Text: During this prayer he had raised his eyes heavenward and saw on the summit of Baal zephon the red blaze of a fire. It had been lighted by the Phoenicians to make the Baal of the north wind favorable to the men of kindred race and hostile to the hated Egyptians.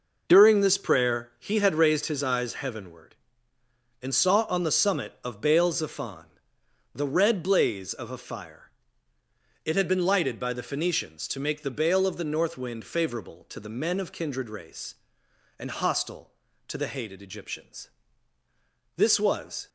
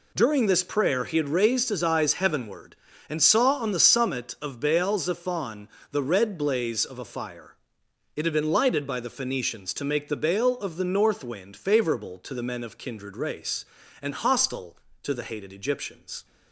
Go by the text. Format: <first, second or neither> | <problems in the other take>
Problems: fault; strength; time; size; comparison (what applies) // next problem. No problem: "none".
second | pauses between "zephon" and "the"; noticeable; at 6.2 s; 0.66 s long; slight in the second // goes on to say "This was"; noticeable; from 18.9 s on; 0.72 s long